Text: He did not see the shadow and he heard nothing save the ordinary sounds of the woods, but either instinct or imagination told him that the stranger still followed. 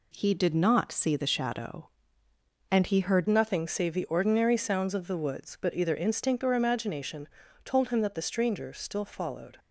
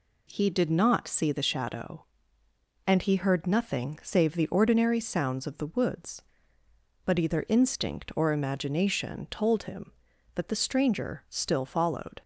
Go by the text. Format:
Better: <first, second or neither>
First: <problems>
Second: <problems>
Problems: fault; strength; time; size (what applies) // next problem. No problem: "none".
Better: second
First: changes voice at "nothing"; from 3.2 s on; 6.3 s long // pauses between "imagination" and "told"; slight; at 7.2 s; 0.34 s long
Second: none